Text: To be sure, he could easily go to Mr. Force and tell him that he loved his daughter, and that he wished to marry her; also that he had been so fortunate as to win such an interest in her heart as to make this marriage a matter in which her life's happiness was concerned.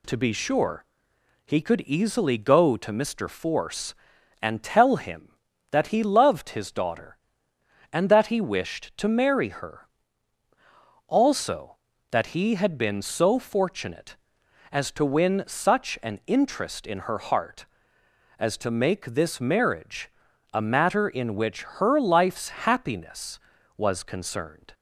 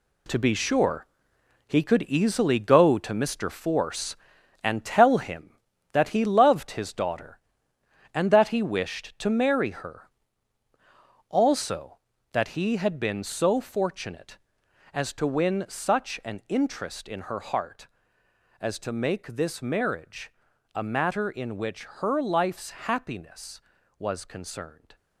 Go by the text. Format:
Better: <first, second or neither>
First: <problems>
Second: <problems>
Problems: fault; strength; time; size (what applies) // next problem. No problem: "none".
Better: first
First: pauses between "marriage" and "a"; at 20.1 s; 0.42 s long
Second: gets quieter; strong; throughout; 9.5 dB // pauses between "marriage" and "a"; at 20.3 s; 0.42 s long